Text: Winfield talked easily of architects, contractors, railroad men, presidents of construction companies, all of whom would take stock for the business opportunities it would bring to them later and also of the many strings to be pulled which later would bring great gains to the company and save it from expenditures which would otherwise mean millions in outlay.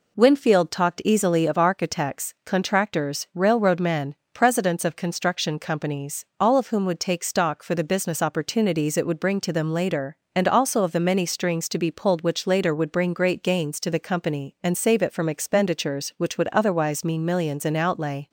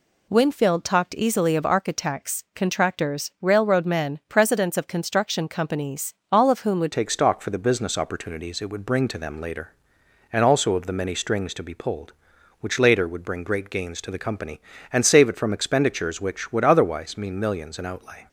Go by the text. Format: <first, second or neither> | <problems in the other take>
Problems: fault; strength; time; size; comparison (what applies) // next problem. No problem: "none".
first | changes voice at "take"; from 6.9 s on; 11.3 s long